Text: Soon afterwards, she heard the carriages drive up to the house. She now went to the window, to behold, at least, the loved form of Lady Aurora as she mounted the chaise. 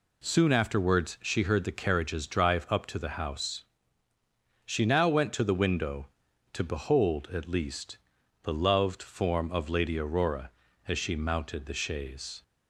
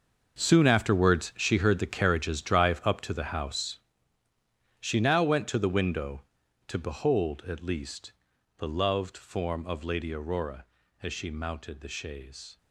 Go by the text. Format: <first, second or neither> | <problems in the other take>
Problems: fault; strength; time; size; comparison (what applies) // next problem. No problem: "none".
first | gets quieter; strong; throughout; 13.5 dB